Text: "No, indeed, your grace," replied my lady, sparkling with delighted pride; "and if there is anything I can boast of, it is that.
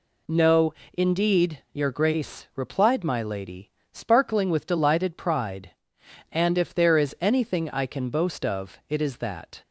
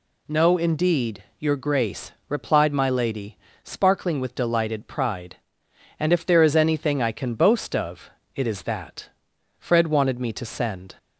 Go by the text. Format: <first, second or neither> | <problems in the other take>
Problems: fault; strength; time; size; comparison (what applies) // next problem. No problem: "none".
first | goes on to say "Fred wanted me to send"; from 9.5 s on; 1.3 s long